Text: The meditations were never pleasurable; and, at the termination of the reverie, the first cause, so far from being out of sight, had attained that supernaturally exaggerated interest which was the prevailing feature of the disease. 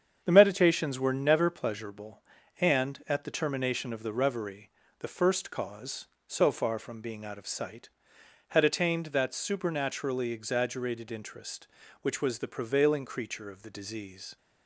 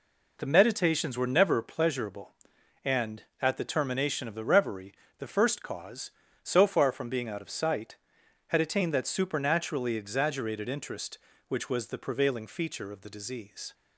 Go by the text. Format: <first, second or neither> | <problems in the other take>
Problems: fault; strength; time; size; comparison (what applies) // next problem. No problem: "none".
second | starts louder than the rest; strong; until 1.2 s; 8 dB // says "creature" for "feature"; at 13.0 s